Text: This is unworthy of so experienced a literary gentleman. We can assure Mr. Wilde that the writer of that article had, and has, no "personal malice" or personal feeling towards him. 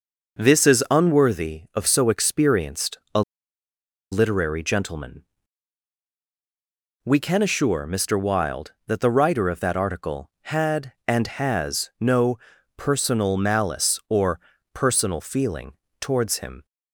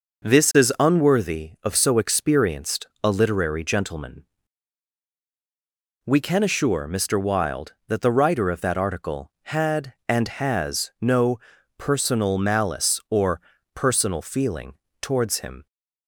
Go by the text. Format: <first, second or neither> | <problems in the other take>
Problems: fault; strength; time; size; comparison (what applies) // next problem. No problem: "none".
second | pauses between "experienced" and "a"; slight; at 2.9 s; 0.16 s long; slight in the second // pauses between "a" and "literary"; noticeable; at 3.2 s; 0.90 s long // pauses between "no" and "personal"; at 12.3 s; 0.40 s long; also in the second // pauses between "or" and "personal"; slight; at 14.3 s; 0.36 s long; slight in the second // pauses between "feeling" and "towards"; slight; at 15.7 s; 0.28 s long; slight in the second